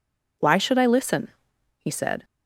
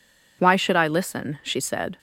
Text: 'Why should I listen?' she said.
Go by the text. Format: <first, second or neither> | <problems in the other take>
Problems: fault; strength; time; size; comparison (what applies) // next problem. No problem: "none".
second | says "he" for "she"; at 1.7 s